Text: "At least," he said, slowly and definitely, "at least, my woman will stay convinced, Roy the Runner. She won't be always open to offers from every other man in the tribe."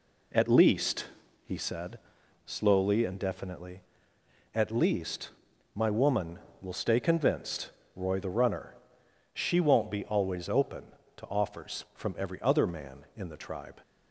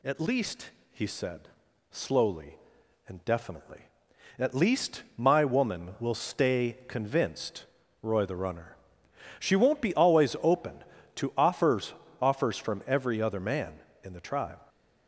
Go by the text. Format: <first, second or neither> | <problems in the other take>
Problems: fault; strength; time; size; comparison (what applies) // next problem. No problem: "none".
first | says "offers" twice; at 12.1 s